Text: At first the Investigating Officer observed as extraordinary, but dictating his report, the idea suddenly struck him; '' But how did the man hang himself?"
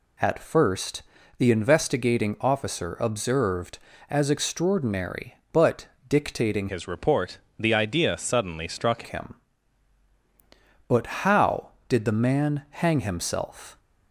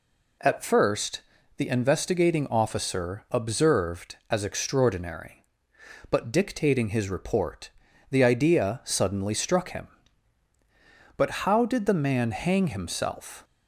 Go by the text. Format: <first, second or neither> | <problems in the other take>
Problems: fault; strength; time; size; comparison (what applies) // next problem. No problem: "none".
second | pauses between "first" and "the"; slight; at 1.0 s; 0.36 s long; slight in the second // pauses between "but" and "dictating"; slight; at 5.8 s; 0.22 s long // changes voice from "his" to "struck"; from 6.6 to 9.0 s; 2.4 s long // pauses between "But" and "how"; slight; at 11.0 s; 0.18 s long; slight in the second